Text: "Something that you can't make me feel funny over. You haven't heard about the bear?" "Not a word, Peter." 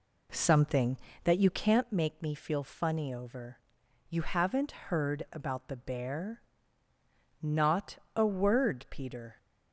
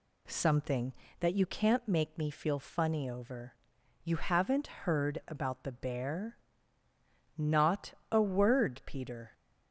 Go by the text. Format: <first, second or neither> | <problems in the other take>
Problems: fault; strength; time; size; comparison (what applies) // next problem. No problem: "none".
second | starts louder than the rest; slight; until 1.9 s; 3 dB // pauses between "Not" and "a"; slight; at 7.9 s; 0.18 s long; slight in the second